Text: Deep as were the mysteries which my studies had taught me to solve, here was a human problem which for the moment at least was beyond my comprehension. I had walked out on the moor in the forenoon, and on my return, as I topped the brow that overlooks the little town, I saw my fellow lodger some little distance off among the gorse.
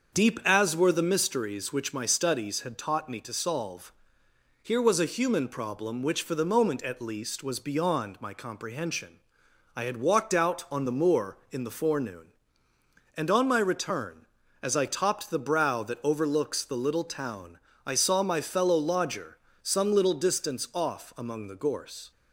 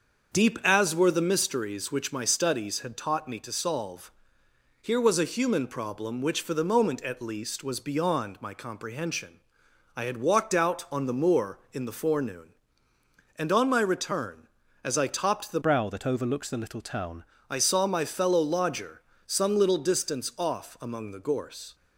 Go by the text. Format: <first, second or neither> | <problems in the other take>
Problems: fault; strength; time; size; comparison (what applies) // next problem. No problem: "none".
first | starts louder than the rest; until 1.3 s; 6.5 dB; also in the first // changes voice from "brow" to "town"; from 15.6 to 17.2 s; 1.6 s long // pauses between "lodger" and "some"; slight; at 19.0 s; 0.26 s long; slight in the first